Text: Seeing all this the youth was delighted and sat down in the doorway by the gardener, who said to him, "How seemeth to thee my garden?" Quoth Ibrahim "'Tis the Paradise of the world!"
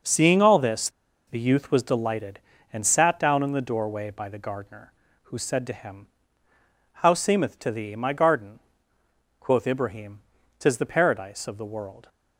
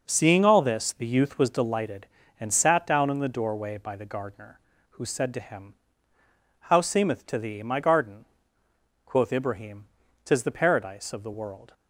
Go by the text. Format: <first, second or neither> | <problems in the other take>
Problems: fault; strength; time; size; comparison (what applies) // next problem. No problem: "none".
second | pauses between "this" and "the"; at 0.8 s; 0.38 s long // pauses between "Ibrahim" and "Tis"; at 10.2 s; 0.40 s long; also in the second